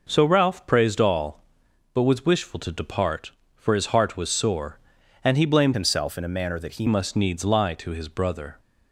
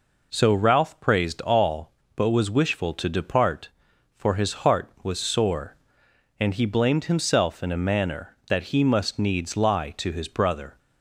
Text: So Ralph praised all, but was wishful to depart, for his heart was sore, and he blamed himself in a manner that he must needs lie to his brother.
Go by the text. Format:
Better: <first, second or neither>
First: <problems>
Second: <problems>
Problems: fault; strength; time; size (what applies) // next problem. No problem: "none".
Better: second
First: changes voice from "himself" to "he"; from 5.7 to 6.8 s; 1.1 s long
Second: none